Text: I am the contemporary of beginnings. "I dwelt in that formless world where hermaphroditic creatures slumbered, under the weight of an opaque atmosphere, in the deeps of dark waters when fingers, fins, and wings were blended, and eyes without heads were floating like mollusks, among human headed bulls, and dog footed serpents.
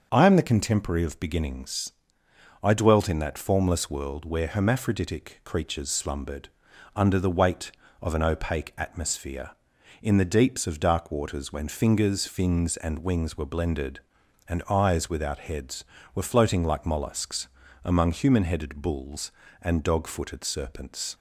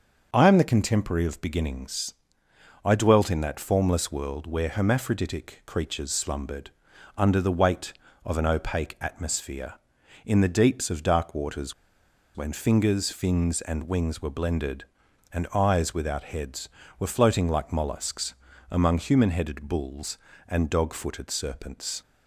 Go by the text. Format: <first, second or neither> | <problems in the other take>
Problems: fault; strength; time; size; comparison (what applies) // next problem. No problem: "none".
first | starts louder than the rest; until 1.3 s; 6.5 dB; also in the first // pauses between "waters" and "when"; noticeable; at 11.7 s; 0.61 s long